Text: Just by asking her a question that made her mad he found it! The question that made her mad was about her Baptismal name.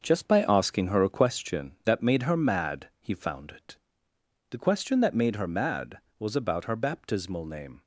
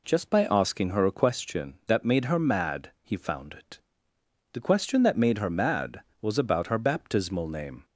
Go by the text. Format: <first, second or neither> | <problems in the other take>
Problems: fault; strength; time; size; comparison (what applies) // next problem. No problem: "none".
second | gets quieter; strong; throughout; 7.5 dB